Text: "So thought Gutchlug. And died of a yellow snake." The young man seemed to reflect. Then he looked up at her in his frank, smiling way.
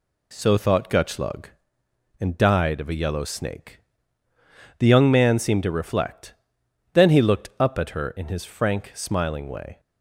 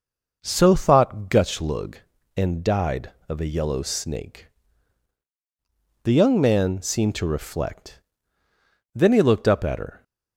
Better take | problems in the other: first | stops before "in his frank smiling way"; at 10.0 s

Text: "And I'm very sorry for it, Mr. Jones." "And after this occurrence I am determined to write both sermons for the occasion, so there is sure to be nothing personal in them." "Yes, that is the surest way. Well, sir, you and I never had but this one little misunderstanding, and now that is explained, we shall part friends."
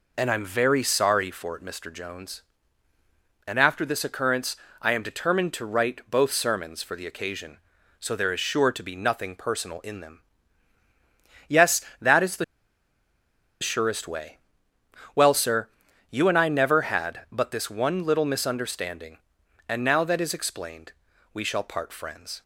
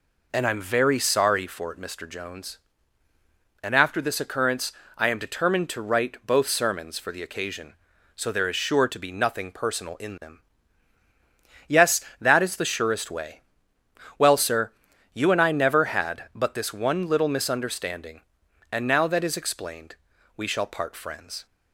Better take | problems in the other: second | pauses between "occurrence" and "I"; slight; at 4.5 s; 0.24 s long; slight in the second // pauses between "the" and "surest"; at 12.4 s; 1.1 s long

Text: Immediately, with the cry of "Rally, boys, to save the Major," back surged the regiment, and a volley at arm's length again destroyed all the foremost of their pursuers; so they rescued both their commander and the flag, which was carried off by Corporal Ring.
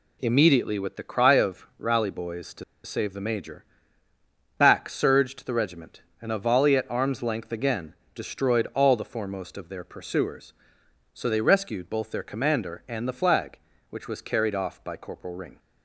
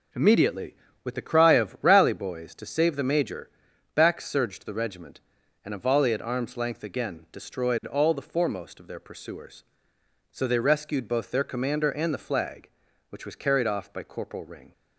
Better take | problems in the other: second | pauses between "to" and "save"; slight; at 2.6 s; 0.22 s long // pauses between "again" and "destroyed"; slight; at 7.9 s; 0.22 s long

